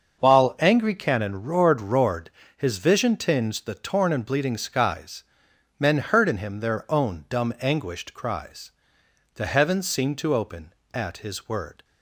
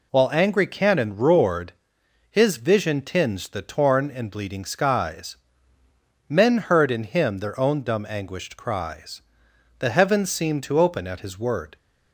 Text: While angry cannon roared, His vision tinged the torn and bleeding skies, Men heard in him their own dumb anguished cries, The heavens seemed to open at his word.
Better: second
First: starts louder than the rest; until 1.2 s; 6.5 dB // says "roared" twice; at 1.7 s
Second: none

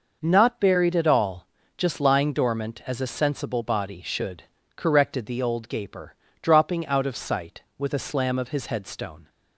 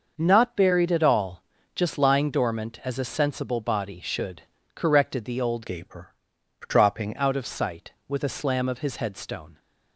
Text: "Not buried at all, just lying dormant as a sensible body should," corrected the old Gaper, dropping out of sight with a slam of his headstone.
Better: first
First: none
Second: starts louder than the rest; noticeable; until 1.1 s; 6 dB // changes voice from "Gaper" to "dropping"; from 5.6 to 7.1 s; 1.5 s long

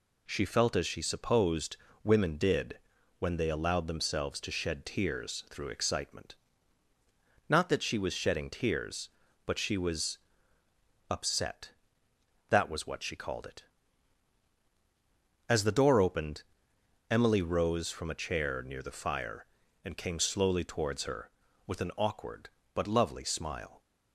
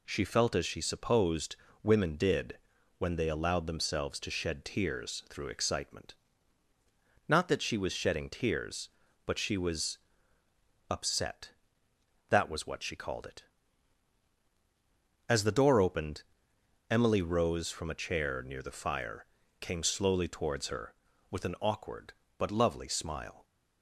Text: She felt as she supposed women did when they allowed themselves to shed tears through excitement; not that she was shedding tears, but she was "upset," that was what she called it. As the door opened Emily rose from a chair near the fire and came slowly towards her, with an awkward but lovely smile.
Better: first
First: pauses between "supposed" and "women"; slight; at 1.7 s; 0.26 s long // pauses between "did" and "when"; at 2.7 s; 0.40 s long // pauses between "was" and "upset"; noticeable; at 10.1 s; 0.90 s long // pauses between "opened" and "Emily"; noticeable; at 16.4 s; 0.66 s long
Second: pauses between "supposed" and "women"; slight; at 1.5 s; 0.26 s long // pauses between "did" and "when"; at 2.5 s; 0.40 s long // pauses between "was" and "upset"; noticeable; at 9.9 s; 0.90 s long // pauses between "opened" and "Emily"; noticeable; at 16.2 s; 0.66 s long // skips "and"; at 19.4 s

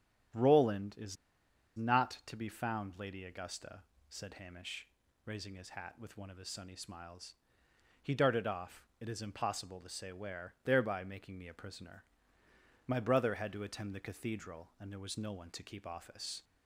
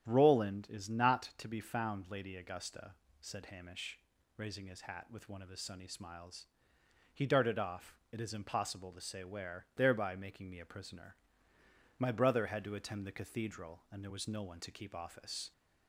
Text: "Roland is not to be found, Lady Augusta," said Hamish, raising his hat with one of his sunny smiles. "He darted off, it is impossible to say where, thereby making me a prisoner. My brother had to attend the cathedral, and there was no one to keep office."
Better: second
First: starts louder than the rest; strong; until 1.9 s; 10 dB // pauses between "is" and "not"; noticeable; at 1.1 s; 0.60 s long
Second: starts louder than the rest; strong; until 1.0 s; 9.5 dB

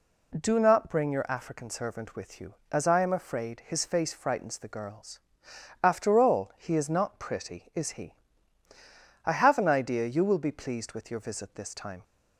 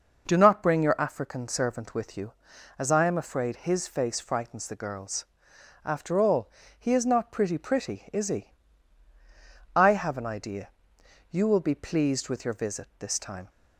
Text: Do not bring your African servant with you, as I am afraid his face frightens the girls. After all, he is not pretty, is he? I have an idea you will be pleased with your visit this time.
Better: first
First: none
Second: says "pretty" twice; at 7.5 s // pauses between "idea" and "you"; noticeable; at 10.7 s; 0.60 s long

